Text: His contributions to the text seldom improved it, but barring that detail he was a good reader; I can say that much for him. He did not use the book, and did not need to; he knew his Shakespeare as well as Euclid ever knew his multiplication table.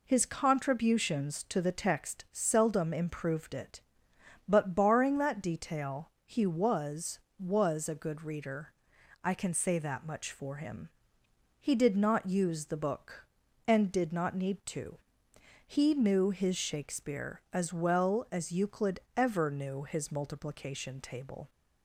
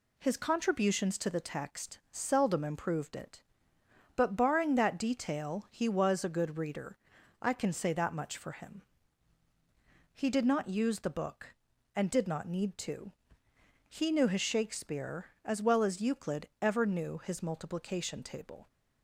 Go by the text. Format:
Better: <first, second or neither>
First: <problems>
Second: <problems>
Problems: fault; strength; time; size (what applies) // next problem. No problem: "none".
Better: second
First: pauses between "detail" and "he"; slight; at 6.0 s; 0.16 s long // says "was" twice; at 7.3 s // pauses between "Euclid" and "ever"; slight; at 18.9 s; 0.18 s long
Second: none